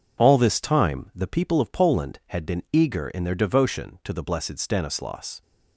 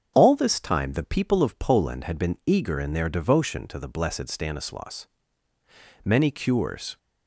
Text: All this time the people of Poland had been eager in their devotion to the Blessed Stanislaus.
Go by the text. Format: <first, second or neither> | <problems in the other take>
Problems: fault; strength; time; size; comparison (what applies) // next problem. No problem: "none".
first | starts louder than the rest; strong; until 1.1 s; 7.5 dB; also in the first // goes on to say "Many cures"; noticeable; from 6.0 s on; 0.92 s long